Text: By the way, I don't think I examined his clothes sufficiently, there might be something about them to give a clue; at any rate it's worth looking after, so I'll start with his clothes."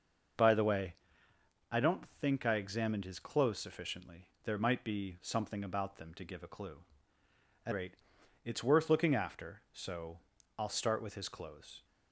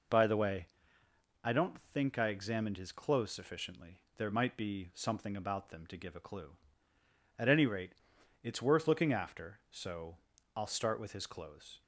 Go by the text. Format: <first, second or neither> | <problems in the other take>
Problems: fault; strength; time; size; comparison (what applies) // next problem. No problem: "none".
second | skips "any"; at 7.7 s // pauses between "rate" and "it's"; noticeable; at 7.9 s; 0.50 s long; noticeable in the second // pauses between "so" and "I'll"; at 10.1 s; 0.40 s long; also in the second